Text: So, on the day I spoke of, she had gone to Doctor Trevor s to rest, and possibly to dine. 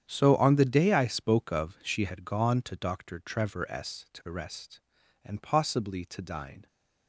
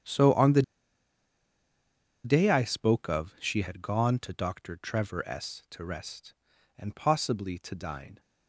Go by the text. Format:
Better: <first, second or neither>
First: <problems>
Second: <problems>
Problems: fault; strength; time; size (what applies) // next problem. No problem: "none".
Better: first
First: starts louder than the rest; strong; until 1.0 s; 9 dB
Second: starts louder than the rest; strong; until 2.6 s; 9 dB // pauses between "the" and "day"; strong; at 0.6 s; 1.6 s long